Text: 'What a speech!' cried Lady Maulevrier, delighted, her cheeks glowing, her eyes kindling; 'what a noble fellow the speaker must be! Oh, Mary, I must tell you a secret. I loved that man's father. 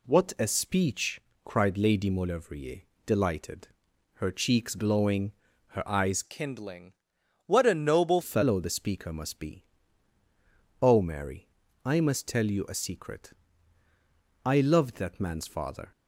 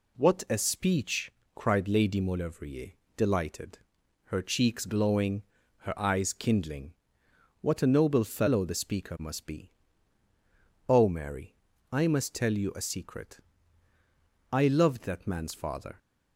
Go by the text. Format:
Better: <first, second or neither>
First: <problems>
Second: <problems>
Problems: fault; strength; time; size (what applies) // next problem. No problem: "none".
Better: second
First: changes voice from "kindling" to "noble"; from 6.2 to 8.2 s; 2.0 s long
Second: none